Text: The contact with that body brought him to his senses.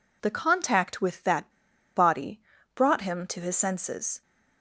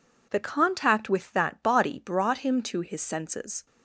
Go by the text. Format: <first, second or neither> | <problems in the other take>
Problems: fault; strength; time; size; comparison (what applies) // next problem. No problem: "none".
second | pauses between "that" and "body"; noticeable; at 1.4 s; 0.47 s long // pauses between "body" and "brought"; slight; at 2.3 s; 0.36 s long